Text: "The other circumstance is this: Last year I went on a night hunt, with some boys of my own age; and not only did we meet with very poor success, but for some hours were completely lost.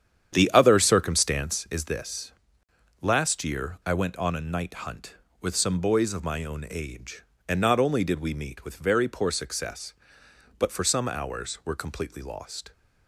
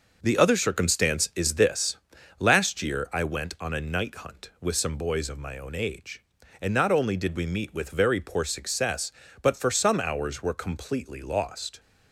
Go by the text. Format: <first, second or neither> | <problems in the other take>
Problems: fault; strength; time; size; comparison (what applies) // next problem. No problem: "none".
second | starts louder than the rest; strong; until 1.6 s; 9 dB